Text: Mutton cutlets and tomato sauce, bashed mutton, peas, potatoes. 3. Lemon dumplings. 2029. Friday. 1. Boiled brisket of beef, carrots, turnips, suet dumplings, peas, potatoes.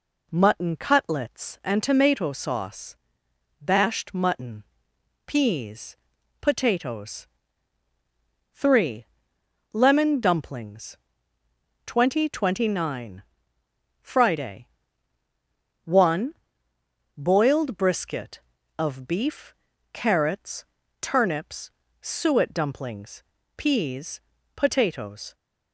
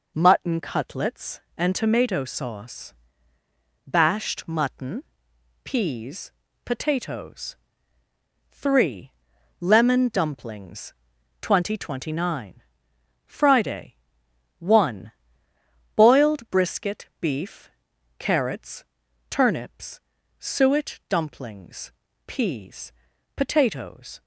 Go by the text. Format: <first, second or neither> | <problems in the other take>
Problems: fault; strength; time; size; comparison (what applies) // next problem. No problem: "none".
first | skips "of"; at 17.1 s